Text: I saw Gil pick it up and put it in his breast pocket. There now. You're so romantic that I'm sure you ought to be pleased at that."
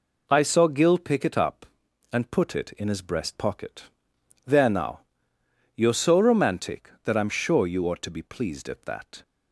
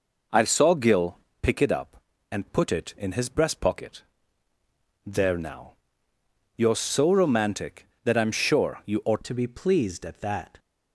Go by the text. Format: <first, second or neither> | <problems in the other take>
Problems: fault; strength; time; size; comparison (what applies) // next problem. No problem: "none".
first | pauses between "Gil" and "pick"; slight; at 1.1 s; 0.24 s long // changes voice at "to"; from 9.2 s on; 1.3 s long